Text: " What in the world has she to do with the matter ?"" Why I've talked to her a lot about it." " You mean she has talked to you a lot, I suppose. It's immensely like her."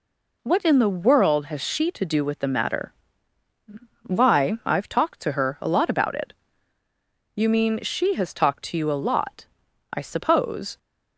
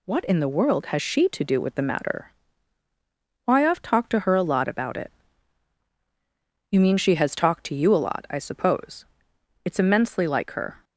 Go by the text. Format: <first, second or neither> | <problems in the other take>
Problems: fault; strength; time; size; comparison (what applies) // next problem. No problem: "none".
second | stops before "It's immensely like her"; at 10.7 s